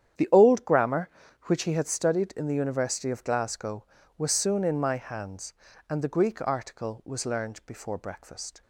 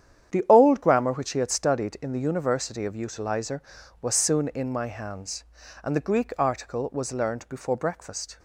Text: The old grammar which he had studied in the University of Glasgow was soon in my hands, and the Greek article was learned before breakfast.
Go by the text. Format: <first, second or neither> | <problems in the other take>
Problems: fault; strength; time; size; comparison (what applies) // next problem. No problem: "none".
first | starts louder than the rest; strong; until 1.3 s; 9.5 dB; strong in the first // says "Utilizer" for "Glasgow"; at 2.9 s